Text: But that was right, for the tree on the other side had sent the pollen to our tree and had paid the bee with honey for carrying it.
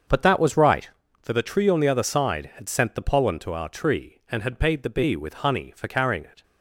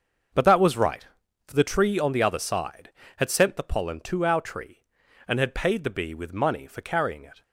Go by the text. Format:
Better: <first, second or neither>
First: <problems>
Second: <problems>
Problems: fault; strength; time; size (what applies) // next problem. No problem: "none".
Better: first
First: starts louder than the rest; until 1.4 s; 7 dB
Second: starts louder than the rest; until 1.7 s; 6.5 dB // says "money" for "honey"; at 6.3 s